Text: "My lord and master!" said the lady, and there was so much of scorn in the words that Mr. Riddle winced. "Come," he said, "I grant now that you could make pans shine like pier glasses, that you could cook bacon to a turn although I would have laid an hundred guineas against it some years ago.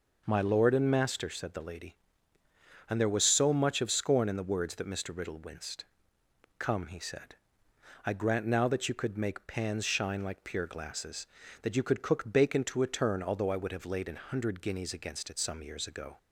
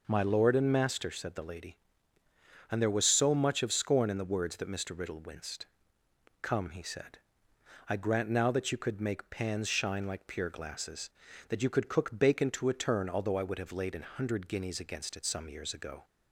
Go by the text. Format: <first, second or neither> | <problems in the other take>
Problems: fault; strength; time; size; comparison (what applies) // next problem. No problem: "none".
neither | none